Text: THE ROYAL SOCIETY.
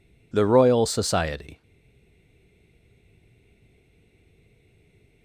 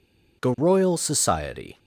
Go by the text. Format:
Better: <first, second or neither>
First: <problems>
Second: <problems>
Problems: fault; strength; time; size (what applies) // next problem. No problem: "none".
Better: second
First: stays silent after the last word; strong; from 1.6 s on; 3.6 s long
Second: none